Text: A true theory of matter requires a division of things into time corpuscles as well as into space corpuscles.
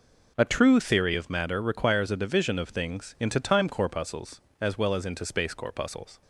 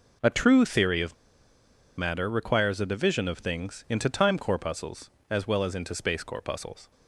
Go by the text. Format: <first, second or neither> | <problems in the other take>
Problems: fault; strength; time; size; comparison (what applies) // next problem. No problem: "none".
first | pauses between "of" and "matter"; noticeable; at 1.1 s; 0.82 s long